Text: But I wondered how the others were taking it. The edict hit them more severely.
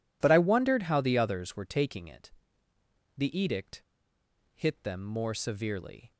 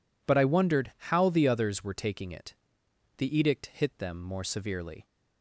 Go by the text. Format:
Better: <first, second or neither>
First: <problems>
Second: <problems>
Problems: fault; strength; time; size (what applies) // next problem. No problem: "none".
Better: second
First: pauses between "edict" and "hit"; noticeable; at 3.8 s; 0.71 s long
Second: none